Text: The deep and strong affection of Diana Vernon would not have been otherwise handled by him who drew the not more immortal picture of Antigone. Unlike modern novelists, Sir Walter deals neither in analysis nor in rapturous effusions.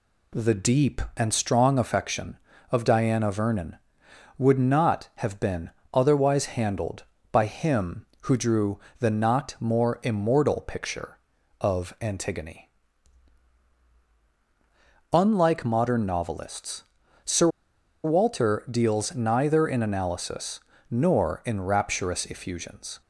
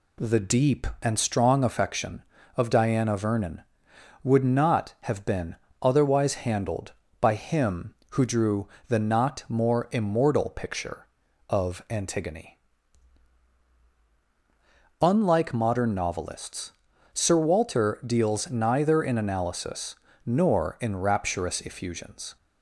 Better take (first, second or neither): second